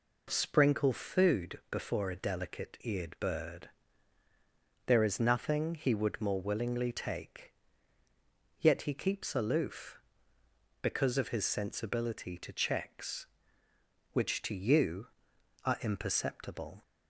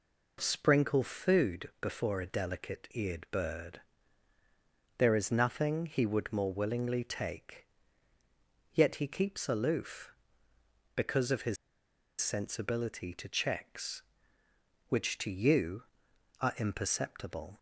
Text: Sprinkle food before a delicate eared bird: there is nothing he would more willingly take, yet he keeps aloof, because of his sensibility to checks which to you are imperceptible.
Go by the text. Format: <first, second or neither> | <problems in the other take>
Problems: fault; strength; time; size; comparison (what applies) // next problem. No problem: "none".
first | pauses between "his" and "sensibility"; noticeable; at 11.5 s; 0.65 s long